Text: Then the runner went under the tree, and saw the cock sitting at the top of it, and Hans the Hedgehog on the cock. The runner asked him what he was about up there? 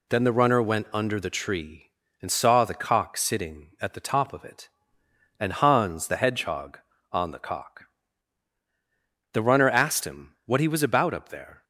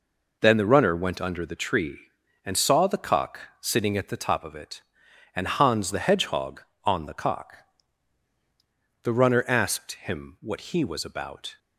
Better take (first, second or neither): first